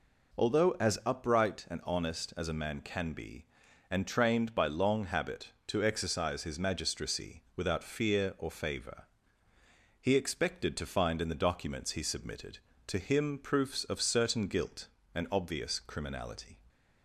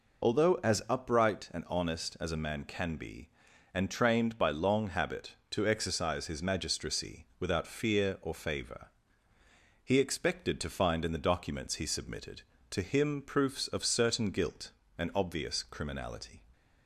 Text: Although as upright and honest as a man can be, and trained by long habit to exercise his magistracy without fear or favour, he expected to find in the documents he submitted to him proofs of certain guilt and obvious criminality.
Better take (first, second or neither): first